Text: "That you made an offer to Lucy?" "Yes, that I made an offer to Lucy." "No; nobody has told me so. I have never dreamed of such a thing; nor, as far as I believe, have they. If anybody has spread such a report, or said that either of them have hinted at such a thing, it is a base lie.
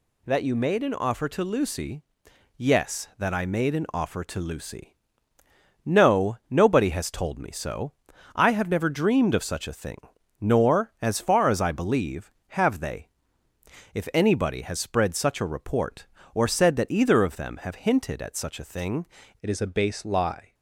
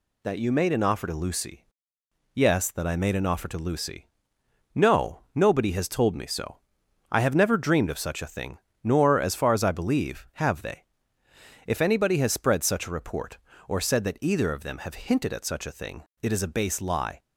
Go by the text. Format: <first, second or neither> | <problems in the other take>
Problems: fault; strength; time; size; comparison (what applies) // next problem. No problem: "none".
second | changes voice at "it"; from 19.4 s on; 1.1 s long